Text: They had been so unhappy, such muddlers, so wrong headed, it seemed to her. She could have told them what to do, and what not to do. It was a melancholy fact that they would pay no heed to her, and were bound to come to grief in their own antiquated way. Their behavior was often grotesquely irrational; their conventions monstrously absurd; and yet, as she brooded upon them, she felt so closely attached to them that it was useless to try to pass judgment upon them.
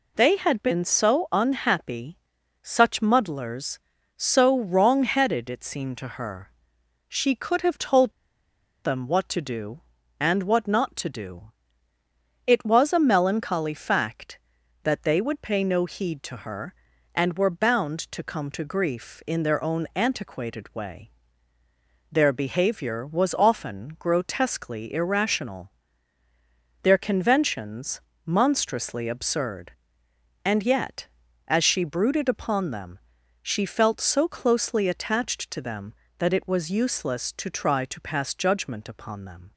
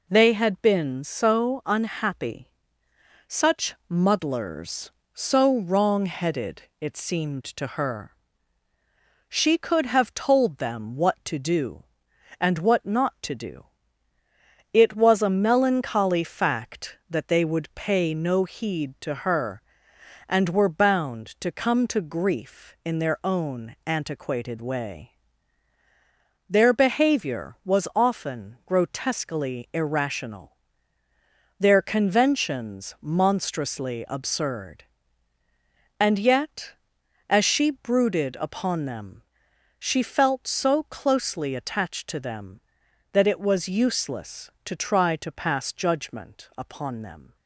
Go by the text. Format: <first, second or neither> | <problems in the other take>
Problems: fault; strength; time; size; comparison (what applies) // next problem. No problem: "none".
second | pauses between "told" and "them"; noticeable; at 8.1 s; 0.72 s long // pauses between "conventions" and "monstrously"; slight; at 28.0 s; 0.26 s long